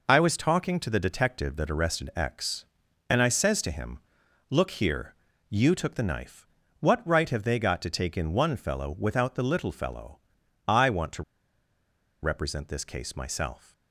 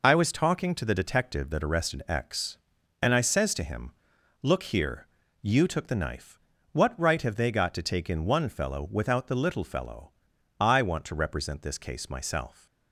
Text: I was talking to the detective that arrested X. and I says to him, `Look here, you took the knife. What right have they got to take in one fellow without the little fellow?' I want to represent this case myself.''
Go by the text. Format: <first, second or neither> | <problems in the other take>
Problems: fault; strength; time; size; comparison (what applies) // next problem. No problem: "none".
second | pauses between "to" and "represent"; at 11.2 s; 0.99 s long